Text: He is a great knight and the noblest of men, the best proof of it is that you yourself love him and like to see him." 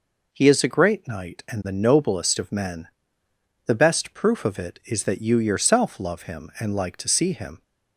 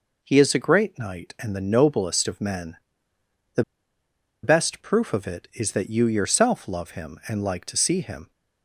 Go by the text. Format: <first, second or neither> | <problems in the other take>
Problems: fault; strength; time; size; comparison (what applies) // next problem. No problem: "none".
first | pauses between "the" and "best"; noticeable; at 3.6 s; 0.80 s long